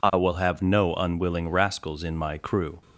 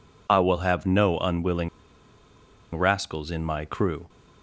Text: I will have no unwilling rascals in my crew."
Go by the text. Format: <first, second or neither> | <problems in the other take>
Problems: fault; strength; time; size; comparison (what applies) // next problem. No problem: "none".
first | pauses between "unwilling" and "rascals"; at 1.6 s; 1.0 s long